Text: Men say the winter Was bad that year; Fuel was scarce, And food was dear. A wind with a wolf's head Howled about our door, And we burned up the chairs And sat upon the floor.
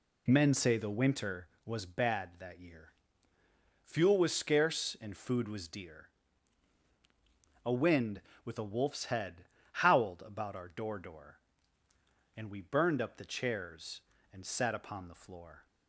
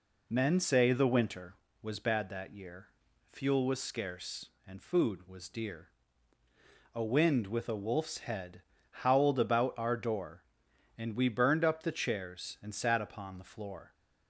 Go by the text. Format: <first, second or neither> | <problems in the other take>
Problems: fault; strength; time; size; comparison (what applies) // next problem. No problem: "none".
second | pauses between "head" and "Howled"; slight; at 9.4 s; 0.26 s long; slight in the second // says "door" twice; at 10.9 s